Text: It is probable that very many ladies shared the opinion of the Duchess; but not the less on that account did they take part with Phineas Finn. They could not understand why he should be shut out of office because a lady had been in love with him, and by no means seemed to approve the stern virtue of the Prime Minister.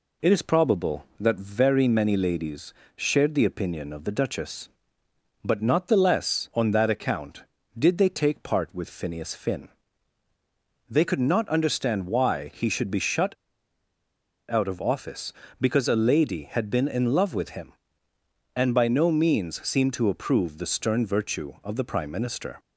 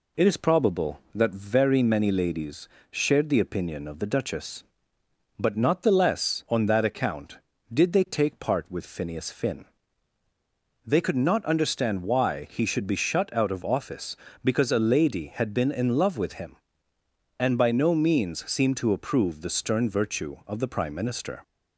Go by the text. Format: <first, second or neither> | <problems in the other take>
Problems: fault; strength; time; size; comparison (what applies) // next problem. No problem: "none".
second | pauses between "ladies" and "shared"; slight; at 2.7 s; 0.24 s long; slight in the second // pauses between "shut" and "out"; at 13.3 s; 1.1 s long